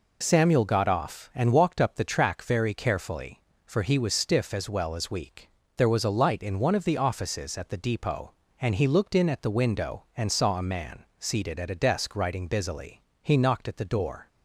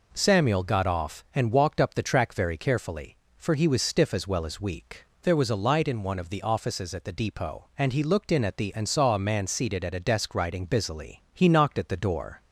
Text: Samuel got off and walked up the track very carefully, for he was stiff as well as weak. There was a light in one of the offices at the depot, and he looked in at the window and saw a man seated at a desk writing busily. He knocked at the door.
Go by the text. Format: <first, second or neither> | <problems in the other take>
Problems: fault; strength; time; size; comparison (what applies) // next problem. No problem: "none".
first | skips "window"; at 8.7 s